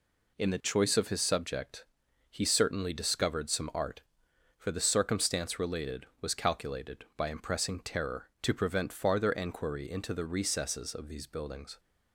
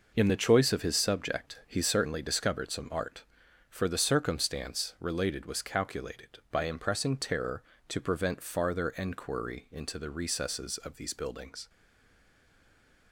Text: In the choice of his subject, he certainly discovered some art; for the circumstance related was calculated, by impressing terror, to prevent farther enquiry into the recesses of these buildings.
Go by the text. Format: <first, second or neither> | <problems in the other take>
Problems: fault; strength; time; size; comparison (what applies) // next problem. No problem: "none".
first | stays silent after the last word; noticeable; from 11.6 s on; 1.5 s long